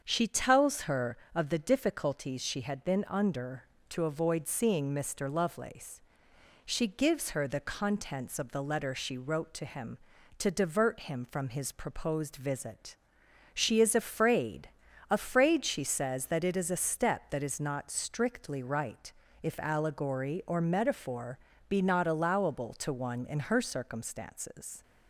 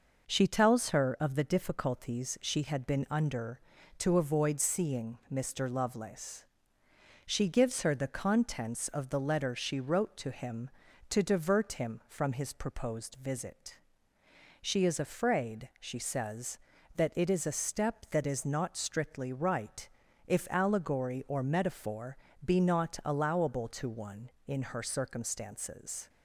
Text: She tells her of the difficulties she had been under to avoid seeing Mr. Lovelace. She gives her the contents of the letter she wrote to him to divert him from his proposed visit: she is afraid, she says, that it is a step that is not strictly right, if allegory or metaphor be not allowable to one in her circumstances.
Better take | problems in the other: second | starts louder than the rest; strong; until 1.0 s; 7 dB // says "afraid" twice; at 15.1 s // pauses between "metaphor" and "be"; slight; at 21.3 s; 0.30 s long; slight in the second

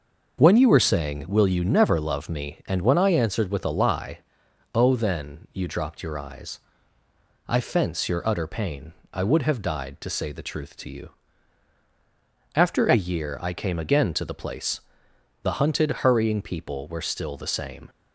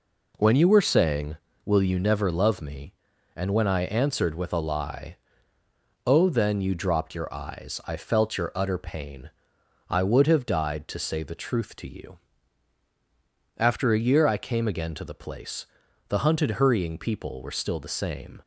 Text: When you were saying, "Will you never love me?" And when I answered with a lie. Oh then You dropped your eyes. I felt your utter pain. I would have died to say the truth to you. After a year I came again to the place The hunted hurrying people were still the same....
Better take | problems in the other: second | starts louder than the rest; noticeable; until 1.4 s; 6 dB // says "fence" for "felt"; at 7.5 s // pauses between "place" and "The"; noticeable; at 14.7 s; 0.62 s long; also in the second

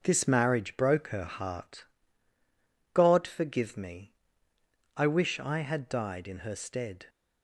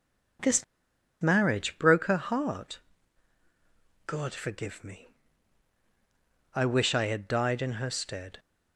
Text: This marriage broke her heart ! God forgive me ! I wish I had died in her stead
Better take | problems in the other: first | pauses between "This" and "marriage"; noticeable; at 0.6 s; 0.56 s long

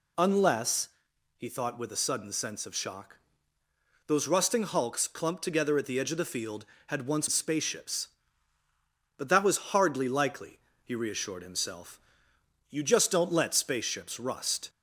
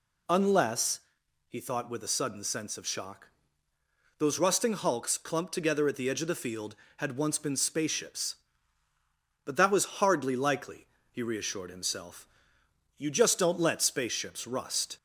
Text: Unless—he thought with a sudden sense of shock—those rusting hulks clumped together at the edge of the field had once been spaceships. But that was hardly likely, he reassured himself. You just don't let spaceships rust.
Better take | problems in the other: second | skips "been"; at 7.2 s

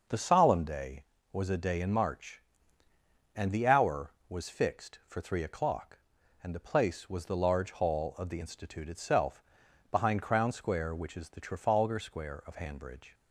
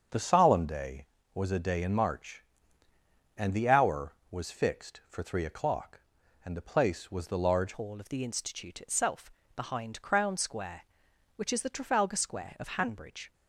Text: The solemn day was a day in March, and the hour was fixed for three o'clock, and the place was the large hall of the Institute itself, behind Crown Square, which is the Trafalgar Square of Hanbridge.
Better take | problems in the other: first | starts louder than the rest; until 1.3 s; 7 dB // changes voice at "hall"; from 7.7 s on; 5.6 s long

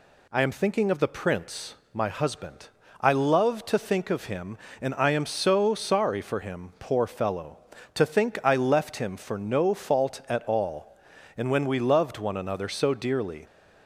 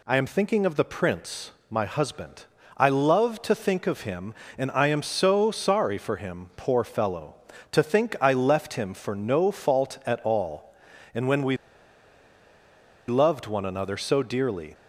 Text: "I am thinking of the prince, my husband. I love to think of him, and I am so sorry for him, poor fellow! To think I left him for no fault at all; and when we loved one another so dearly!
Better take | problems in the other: first | pauses between "we" and "loved"; strong; at 11.5 s; 1.5 s long

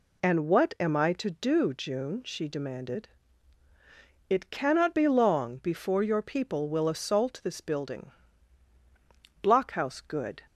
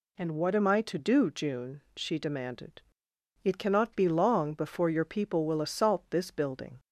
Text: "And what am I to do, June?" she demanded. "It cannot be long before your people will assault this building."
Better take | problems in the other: second | goes on to say "Blockhouse good"; noticeable; from 9.4 s on; 0.98 s long

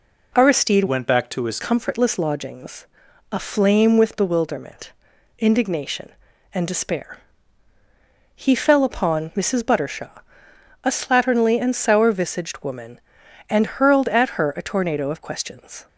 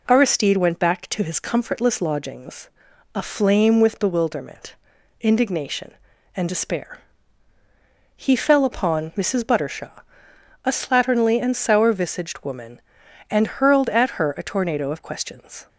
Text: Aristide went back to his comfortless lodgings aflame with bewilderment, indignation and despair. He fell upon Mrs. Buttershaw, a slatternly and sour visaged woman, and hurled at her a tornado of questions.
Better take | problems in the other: second | changes voice from "went" to "his"; from 0.8 to 1.5 s; 0.7 s long // pauses between "lodgings" and "aflame"; at 2.8 s; 0.44 s long; also in the second

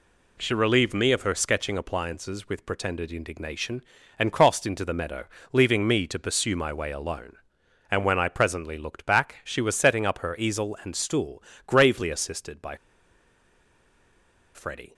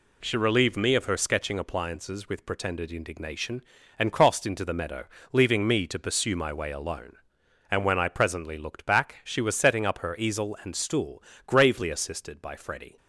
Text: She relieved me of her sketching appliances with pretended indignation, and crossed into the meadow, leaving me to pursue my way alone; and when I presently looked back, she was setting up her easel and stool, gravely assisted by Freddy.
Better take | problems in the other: second | pauses between "by" and "Freddy"; strong; at 12.7 s; 1.7 s long

